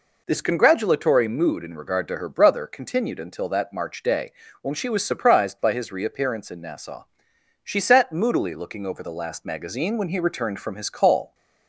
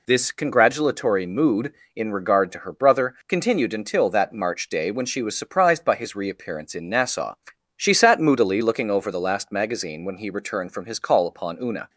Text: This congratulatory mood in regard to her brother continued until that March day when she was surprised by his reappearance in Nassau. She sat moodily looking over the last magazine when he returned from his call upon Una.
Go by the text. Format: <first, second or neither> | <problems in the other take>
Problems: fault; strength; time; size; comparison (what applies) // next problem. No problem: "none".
second | pauses between "day" and "when"; slight; at 4.3 s; 0.30 s long // stops before "upon Una"; at 11.3 s